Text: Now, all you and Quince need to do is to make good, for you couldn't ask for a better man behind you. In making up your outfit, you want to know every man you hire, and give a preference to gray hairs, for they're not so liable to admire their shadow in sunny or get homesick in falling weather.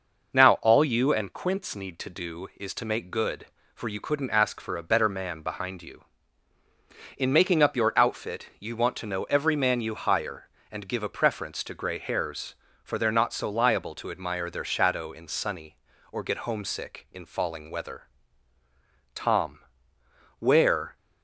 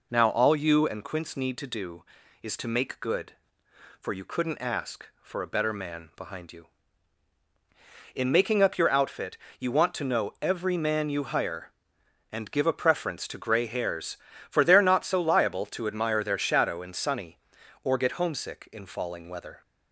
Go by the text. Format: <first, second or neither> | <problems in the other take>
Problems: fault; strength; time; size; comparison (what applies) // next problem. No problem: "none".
second | goes on to say "Tom where"; strong; from 19.1 s on; 1.8 s long